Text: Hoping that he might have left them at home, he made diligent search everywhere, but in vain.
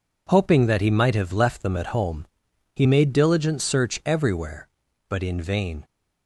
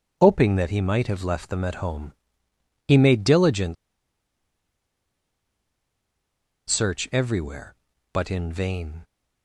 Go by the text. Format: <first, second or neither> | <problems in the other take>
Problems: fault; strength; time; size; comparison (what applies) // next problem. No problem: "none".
first | pauses between "diligent" and "search"; strong; at 3.7 s; 2.9 s long